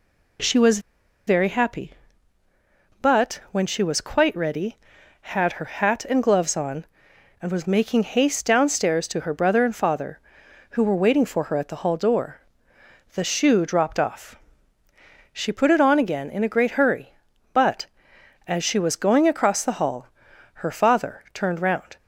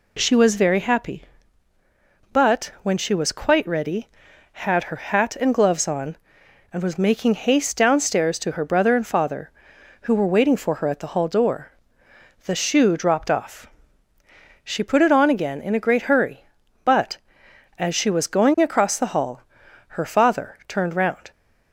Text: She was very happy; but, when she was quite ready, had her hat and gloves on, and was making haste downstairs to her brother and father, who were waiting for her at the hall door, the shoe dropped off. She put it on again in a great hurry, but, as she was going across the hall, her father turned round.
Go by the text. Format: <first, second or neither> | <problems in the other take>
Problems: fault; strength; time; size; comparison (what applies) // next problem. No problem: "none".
second | pauses between "was" and "very"; noticeable; at 0.7 s; 0.48 s long